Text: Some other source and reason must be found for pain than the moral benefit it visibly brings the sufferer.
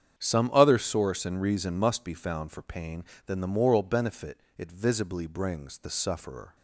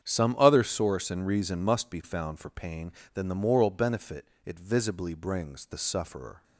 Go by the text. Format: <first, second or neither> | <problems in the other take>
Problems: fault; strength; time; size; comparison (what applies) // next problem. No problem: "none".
neither | starts louder than the rest; strong; the same in both // pauses between "benefit" and "it"; slight; the same in both